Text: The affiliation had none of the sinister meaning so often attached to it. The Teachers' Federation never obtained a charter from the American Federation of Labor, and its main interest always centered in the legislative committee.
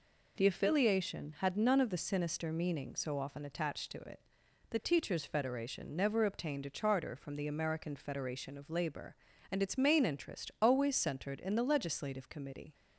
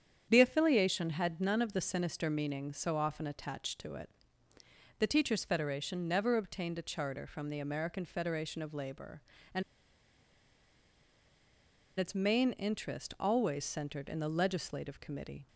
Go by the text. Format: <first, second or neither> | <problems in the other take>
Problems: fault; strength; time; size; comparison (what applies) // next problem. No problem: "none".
first | starts louder than the rest; strong; until 1.2 s; 8.5 dB // pauses between "and" and "its"; strong; at 9.6 s; 2.3 s long